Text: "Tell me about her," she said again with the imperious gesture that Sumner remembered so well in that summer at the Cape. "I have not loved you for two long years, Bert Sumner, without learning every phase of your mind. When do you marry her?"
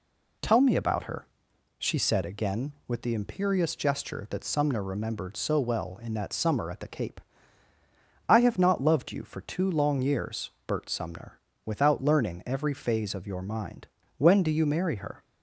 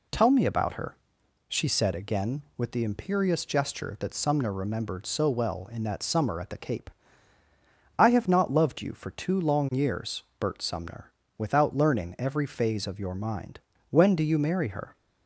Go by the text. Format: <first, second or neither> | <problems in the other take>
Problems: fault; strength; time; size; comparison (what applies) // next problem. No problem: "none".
neither | none